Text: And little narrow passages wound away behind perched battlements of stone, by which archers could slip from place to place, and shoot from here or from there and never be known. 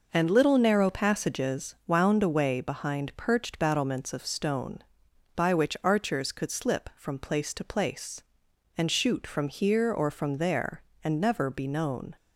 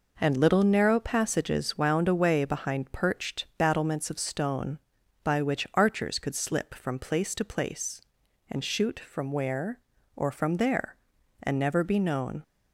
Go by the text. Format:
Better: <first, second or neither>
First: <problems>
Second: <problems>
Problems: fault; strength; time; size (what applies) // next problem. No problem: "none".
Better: first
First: none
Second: says "where" for "here"; at 9.3 s